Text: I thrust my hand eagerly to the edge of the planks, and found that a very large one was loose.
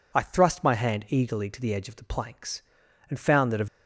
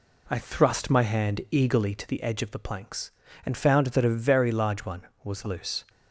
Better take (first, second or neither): second